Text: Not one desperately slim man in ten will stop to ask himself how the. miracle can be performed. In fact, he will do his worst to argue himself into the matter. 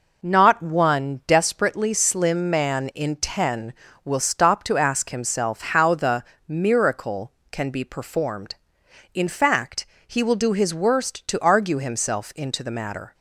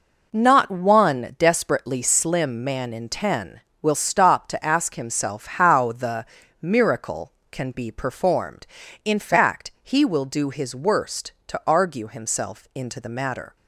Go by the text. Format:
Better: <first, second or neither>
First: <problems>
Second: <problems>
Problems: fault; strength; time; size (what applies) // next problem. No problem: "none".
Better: neither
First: none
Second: none